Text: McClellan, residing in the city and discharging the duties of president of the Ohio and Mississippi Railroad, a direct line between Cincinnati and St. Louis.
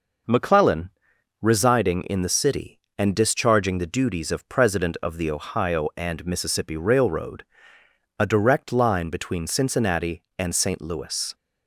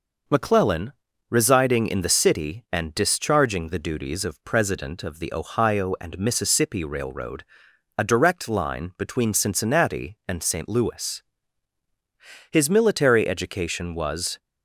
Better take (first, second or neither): first